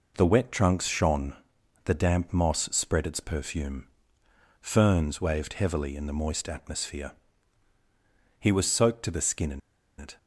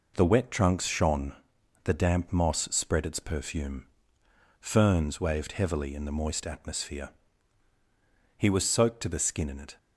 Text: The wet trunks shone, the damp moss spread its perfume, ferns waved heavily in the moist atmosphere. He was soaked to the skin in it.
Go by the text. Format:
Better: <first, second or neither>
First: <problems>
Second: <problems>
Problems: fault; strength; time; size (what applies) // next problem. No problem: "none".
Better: second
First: pauses between "in" and "it"; at 9.5 s; 0.38 s long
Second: none